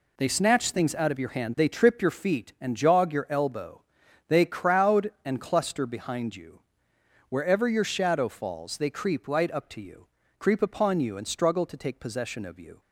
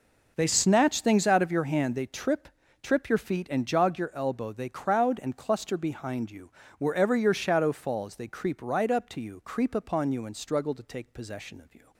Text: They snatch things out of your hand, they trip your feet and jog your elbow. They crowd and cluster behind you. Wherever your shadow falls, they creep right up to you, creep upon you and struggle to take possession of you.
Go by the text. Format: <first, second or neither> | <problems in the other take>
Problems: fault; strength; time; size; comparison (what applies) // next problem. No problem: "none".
first | says "trip" twice; at 2.8 s